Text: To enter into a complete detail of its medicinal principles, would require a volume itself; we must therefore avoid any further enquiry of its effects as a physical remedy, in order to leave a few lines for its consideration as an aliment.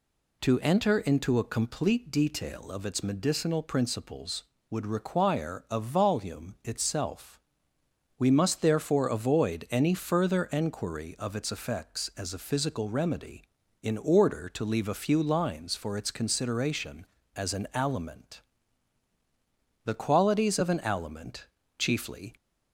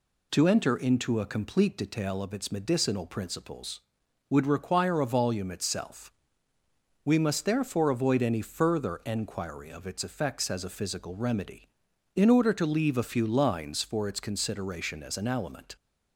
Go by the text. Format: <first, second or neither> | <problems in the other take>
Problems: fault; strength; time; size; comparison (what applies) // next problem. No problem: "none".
second | goes on to say "The qualities of an aliment chiefly"; strong; from 19.8 s on; 2.5 s long